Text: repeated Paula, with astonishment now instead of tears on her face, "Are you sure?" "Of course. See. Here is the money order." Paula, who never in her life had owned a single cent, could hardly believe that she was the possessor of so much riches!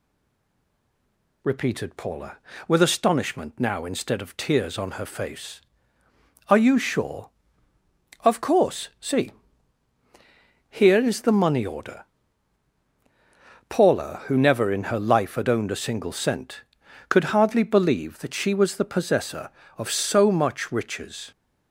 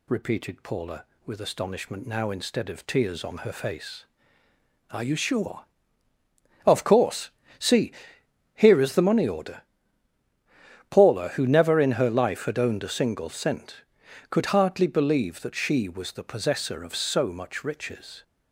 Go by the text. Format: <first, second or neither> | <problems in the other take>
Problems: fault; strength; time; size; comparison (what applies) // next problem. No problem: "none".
second | stays silent before the first word; noticeable; until 1.4 s; 1.4 s long